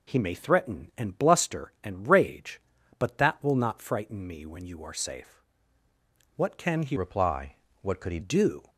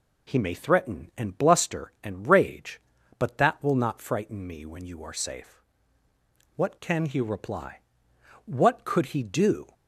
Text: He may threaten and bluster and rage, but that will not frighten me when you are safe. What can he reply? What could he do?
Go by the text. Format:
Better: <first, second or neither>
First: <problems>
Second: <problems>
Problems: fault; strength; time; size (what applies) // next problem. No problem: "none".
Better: second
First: changes voice from "reply" to "he"; from 6.9 to 8.1 s; 1.2 s long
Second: none